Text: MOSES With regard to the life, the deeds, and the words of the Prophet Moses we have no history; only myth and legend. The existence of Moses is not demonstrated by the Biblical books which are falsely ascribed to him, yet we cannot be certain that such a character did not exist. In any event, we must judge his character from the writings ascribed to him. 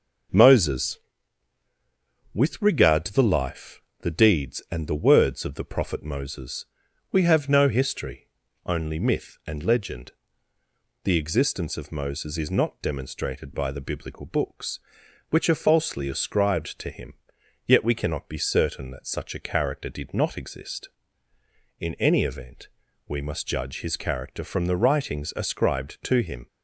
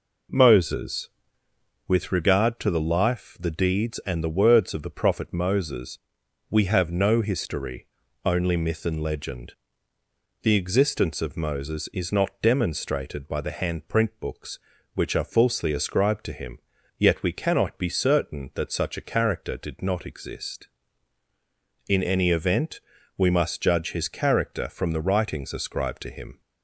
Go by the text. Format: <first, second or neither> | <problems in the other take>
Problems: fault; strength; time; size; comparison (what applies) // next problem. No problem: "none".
first | pauses between "Moses" and "we"; noticeable; at 5.9 s; 0.50 s long; also in the first // says "Handprint" for "Biblical"; at 13.5 s